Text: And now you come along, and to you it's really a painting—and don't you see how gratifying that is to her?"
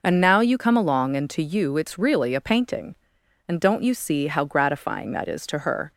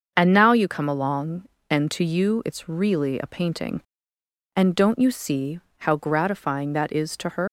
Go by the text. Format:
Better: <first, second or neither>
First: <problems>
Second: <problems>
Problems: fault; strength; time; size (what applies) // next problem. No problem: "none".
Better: first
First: none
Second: starts louder than the rest; until 1.1 s; 6.5 dB // pauses between "see" and "how"; slight; at 5.5 s; 0.18 s long // leaves "her" unfinished; at 7.4 s; 140 ms